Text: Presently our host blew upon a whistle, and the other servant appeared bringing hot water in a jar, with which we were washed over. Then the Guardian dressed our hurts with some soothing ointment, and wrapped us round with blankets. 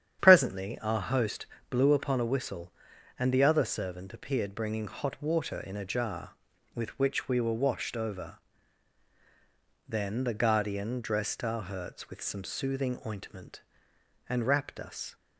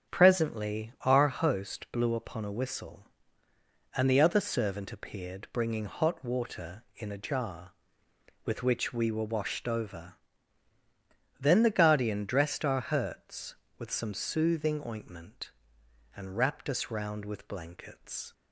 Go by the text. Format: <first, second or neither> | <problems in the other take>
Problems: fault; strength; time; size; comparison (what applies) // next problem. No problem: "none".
second | starts louder than the rest; strong; until 1.2 s; 9 dB; strong in the second // pauses between "host" and "blew"; slight; at 1.4 s; 0.24 s long // stops before "round with blankets"; at 15.1 s